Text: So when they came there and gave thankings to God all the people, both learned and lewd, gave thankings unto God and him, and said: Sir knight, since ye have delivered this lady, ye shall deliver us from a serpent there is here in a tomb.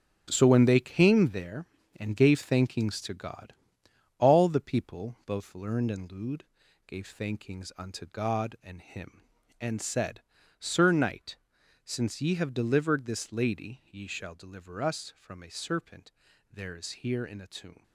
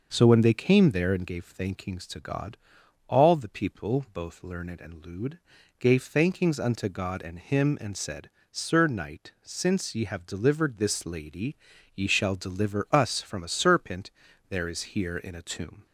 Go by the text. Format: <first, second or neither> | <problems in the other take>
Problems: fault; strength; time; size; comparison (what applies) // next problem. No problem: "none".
second | gets quieter; strong; throughout; 9.5 dB // starts louder than the rest; strong; until 1.3 s; 9 dB; noticeable in the second // pauses between "God" and "all"; noticeable; at 3.5 s; 0.64 s long; noticeable in the second // pauses between "serpent" and "there"; at 16.1 s; 0.42 s long; also in the second